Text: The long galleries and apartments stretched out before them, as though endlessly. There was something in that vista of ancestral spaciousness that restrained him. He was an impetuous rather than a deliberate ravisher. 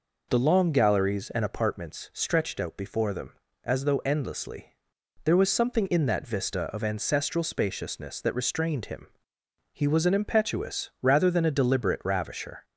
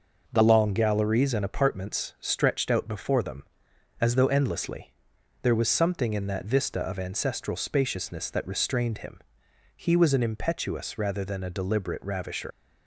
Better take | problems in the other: first | leaves "ravisher" unfinished; at 12.5 s; 100 ms

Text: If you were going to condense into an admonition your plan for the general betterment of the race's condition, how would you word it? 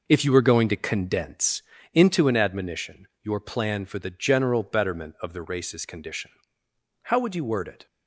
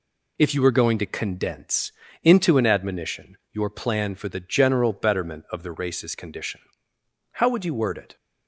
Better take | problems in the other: second | starts louder than the rest; noticeable; until 1.7 s; 5 dB // pauses between "condense" and "into"; slight; at 1.6 s; 0.32 s long; slight in the second

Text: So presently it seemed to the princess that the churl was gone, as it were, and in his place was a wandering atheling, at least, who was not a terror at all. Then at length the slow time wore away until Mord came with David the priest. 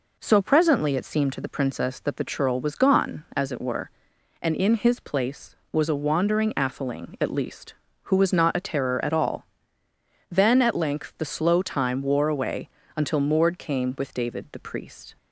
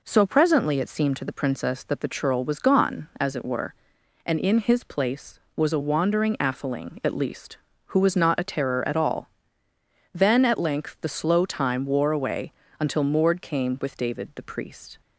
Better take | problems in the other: neither | pauses between "away" and "until"; slight; the same in both

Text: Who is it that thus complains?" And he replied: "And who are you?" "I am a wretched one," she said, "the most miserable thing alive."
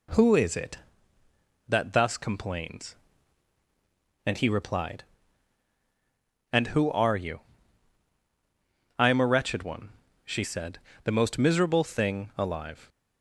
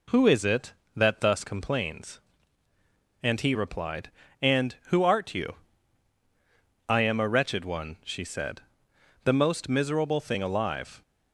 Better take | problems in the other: first | says "art" for "are"; at 5.0 s

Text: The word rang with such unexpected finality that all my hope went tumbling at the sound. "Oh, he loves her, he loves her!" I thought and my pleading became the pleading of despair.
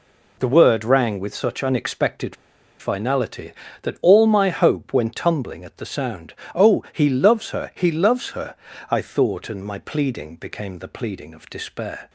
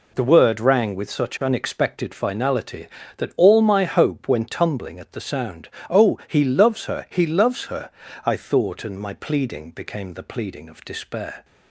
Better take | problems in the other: second | pauses between "unexpected" and "finality"; at 2.3 s; 0.43 s long

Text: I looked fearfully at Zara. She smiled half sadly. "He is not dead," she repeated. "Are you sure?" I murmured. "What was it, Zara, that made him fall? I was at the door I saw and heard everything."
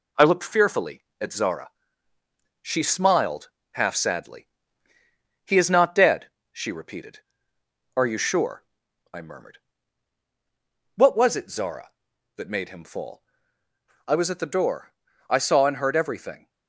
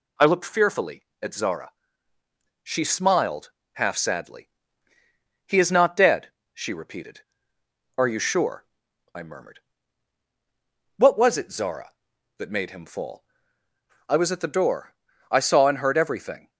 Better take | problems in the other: second | gets quieter; noticeable; throughout; 4 dB // pauses between "smiled" and "half"; slight; at 3.5 s; 0.22 s long; slight in the second // pauses between "door" and "I"; slight; at 14.9 s; 0.34 s long; slight in the second

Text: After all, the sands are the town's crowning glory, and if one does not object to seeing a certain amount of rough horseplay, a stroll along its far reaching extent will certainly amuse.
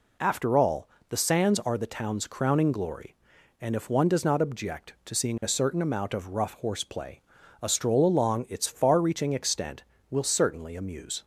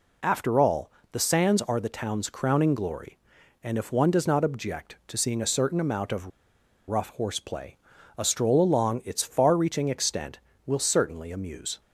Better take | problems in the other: first | pauses between "of" and "rough"; noticeable; at 6.3 s; 0.59 s long

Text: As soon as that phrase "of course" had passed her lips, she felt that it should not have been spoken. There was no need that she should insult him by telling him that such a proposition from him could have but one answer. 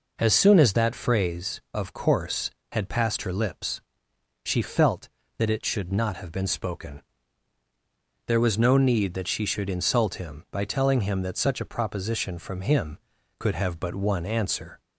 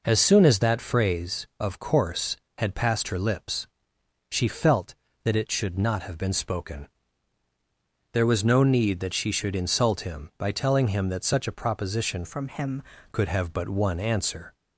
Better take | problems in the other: first | changes voice from "from" to "him"; from 12.2 to 12.8 s; 0.6 s long

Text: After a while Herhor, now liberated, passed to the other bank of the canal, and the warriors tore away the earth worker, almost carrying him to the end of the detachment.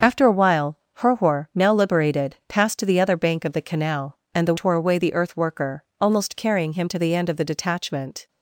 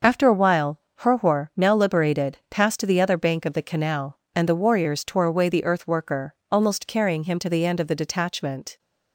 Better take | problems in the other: second | starts louder than the rest; until 1.1 s; 6.5 dB; noticeable in the second // pauses between "while" and "Herhor"; slight; at 0.7 s; 0.16 s long; slight in the second // skips "warriors"; at 4.5 s

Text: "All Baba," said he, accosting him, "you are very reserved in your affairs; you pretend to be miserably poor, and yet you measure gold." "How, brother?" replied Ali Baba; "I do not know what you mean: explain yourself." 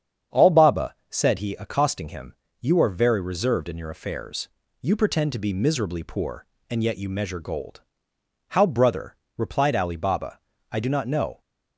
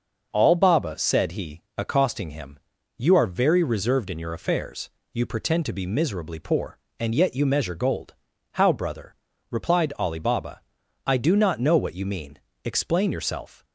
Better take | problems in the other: second | starts louder than the rest; strong; until 1.4 s; 8 dB; noticeable in the second // stops before "what you mean explain yourself"; at 11.4 s

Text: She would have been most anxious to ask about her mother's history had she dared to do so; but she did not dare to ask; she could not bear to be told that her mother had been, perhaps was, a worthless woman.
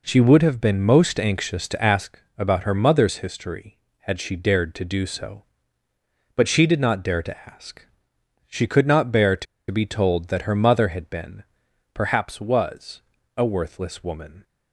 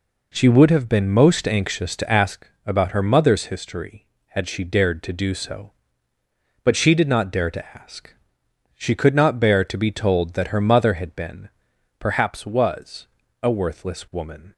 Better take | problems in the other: second | pauses between "ask" and "about"; slight; at 2.2 s; 0.16 s long; slight in the second // pauses between "to" and "be"; slight; at 9.4 s; 0.25 s long

